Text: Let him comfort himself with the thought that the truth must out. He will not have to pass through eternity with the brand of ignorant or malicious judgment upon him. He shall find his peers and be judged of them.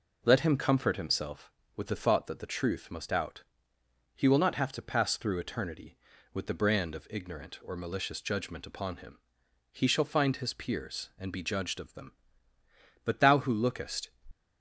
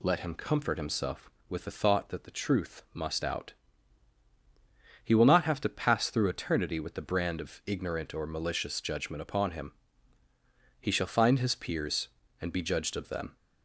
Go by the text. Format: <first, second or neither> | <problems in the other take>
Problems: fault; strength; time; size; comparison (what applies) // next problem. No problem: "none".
second | goes on to say "But thou who lookest"; noticeable; from 13.0 s on; 1.0 s long